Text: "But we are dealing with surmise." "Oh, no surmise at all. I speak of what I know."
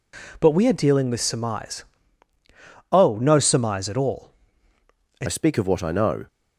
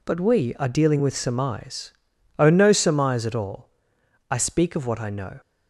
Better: second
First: changes voice at "speak"; from 5.2 s on; 1.0 s long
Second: none

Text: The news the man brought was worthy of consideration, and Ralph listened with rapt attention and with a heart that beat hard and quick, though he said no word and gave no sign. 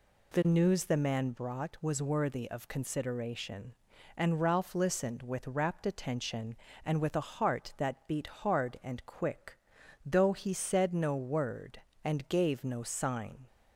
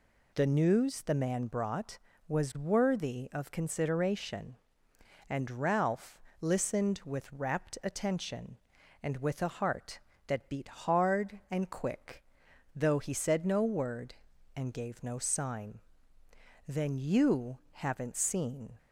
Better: first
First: none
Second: pauses between "Ralph" and "listened"; slight; at 6.1 s; 0.20 s long // goes on to say "Then you haven't seen"; strong; from 16.6 s on; 2.1 s long

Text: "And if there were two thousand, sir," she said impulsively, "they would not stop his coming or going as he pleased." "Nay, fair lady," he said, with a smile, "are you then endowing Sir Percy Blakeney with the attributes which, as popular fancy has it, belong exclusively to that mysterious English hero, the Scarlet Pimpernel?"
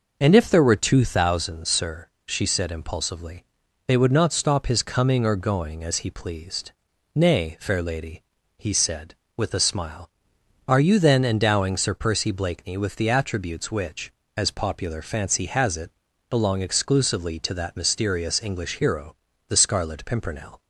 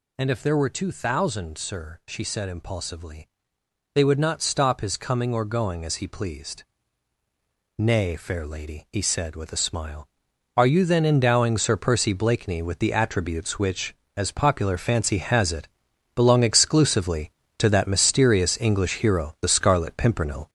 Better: first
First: none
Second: gets louder; throughout; 6.5 dB

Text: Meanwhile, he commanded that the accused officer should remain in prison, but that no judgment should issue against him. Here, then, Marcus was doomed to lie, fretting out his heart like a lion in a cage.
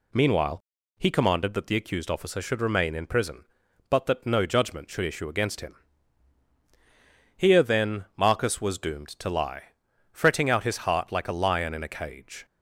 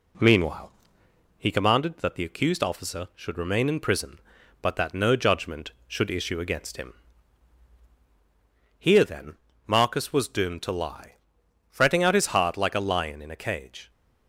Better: neither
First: none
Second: none

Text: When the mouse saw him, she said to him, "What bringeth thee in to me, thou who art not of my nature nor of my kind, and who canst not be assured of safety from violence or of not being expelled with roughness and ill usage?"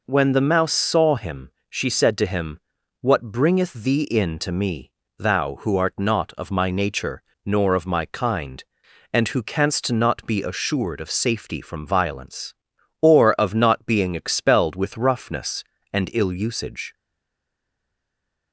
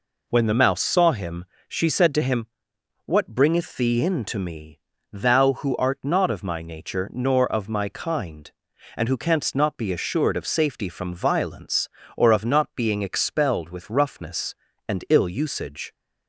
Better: second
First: pauses between "nature" and "nor"; slight; at 7.2 s; 0.22 s long // stays silent after the last word; noticeable; from 16.9 s on; 1.6 s long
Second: none

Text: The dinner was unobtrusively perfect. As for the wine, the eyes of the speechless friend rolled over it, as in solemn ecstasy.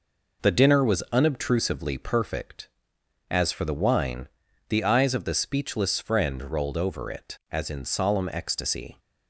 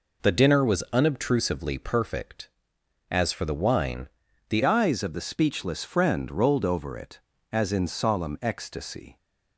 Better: first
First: none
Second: changes voice at "eyes"; from 4.6 s on; 4.5 s long

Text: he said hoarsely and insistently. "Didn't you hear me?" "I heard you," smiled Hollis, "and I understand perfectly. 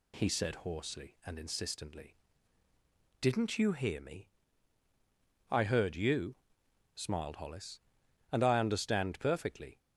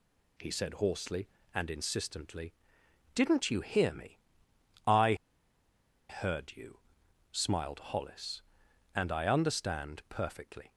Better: first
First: none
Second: pauses between "I" and "heard"; noticeable; at 5.1 s; 0.94 s long

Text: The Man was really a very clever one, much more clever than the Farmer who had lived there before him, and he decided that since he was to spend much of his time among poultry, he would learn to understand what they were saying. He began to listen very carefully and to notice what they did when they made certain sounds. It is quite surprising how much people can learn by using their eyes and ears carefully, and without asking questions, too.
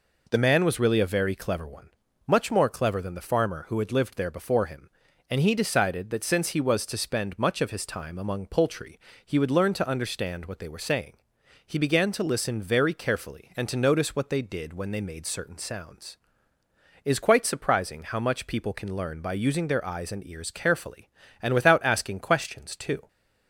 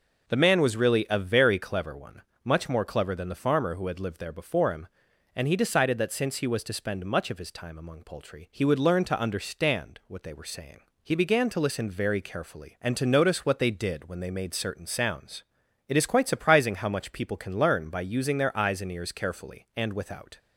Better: first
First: none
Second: stops before "asking questions too"; at 20.3 s

